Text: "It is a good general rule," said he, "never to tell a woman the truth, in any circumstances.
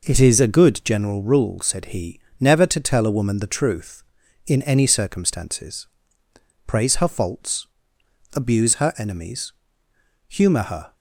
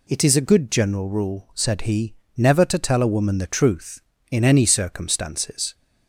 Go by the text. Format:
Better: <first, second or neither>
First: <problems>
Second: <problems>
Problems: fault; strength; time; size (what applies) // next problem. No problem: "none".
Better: second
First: goes on to say "Praise her faults abuse her enemies humour her"; strong; from 6.6 s on; 4.2 s long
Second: none